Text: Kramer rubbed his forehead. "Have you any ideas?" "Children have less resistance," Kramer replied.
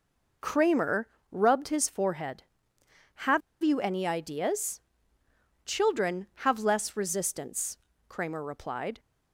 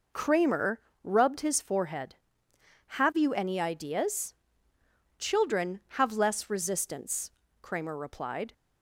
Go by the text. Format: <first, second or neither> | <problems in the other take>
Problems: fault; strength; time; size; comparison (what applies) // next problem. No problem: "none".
second | pauses between "Kramer" and "rubbed"; slight; at 1.0 s; 0.22 s long; slight in the second // pauses between "Have" and "you"; slight; at 3.4 s; 0.22 s long